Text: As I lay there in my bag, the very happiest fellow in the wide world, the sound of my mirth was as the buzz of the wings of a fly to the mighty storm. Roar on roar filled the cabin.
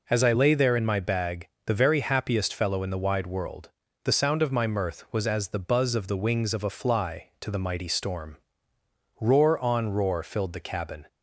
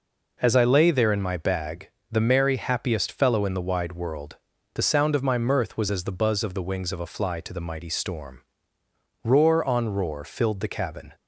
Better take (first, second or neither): first